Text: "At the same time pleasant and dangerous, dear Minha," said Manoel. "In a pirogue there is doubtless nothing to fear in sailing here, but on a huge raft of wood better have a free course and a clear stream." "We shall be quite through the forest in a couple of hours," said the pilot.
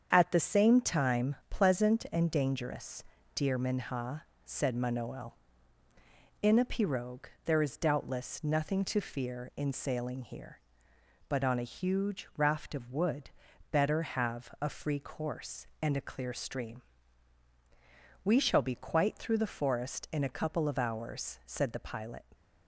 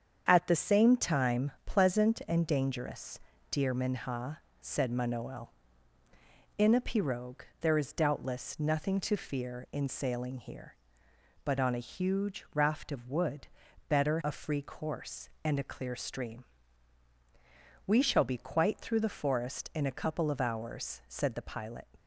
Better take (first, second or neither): first